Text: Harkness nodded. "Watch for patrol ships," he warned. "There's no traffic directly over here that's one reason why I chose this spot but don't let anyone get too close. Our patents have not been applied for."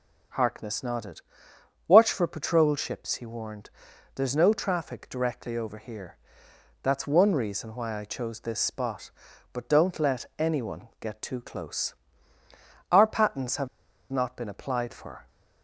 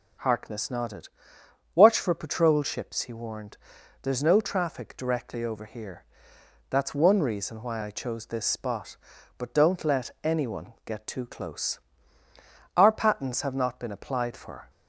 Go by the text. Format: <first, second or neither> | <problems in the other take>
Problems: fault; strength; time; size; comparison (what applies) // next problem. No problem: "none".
second | pauses between "here" and "that's"; noticeable; at 6.1 s; 0.66 s long; noticeable in the second // pauses between "have" and "not"; at 13.6 s; 0.44 s long